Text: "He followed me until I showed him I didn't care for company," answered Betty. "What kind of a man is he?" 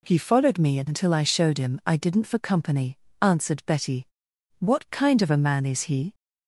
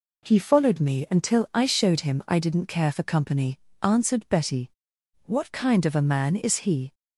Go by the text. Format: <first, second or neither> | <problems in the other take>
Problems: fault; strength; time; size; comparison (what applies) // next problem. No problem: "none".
second | skips "care"; at 2.2 s